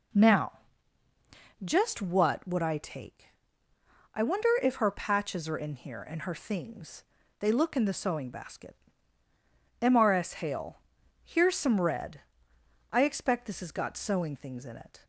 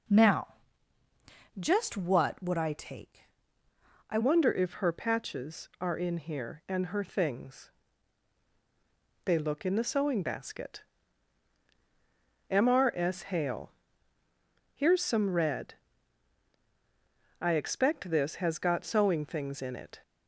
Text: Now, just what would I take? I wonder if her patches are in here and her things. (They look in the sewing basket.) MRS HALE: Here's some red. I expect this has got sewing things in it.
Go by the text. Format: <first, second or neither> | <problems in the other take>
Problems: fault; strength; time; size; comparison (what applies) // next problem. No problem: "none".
first | changes voice at "wonder"; from 4.2 s on; 15.7 s long